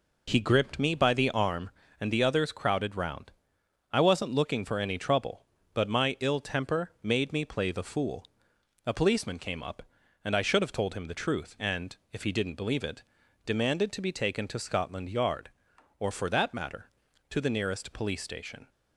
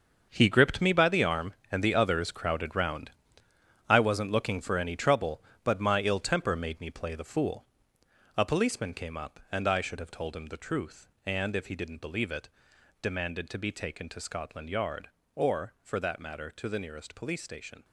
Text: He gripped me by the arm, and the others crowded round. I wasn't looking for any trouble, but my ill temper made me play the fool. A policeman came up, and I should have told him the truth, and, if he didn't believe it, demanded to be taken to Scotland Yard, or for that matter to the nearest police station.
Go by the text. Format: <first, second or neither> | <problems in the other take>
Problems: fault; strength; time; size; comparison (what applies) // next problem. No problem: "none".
first | gets quieter; strong; throughout; 12 dB